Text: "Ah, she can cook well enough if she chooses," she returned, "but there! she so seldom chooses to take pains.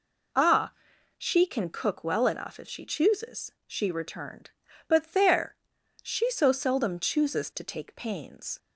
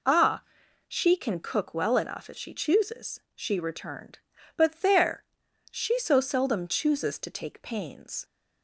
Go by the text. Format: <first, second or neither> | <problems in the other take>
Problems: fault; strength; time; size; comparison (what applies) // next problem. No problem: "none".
neither | none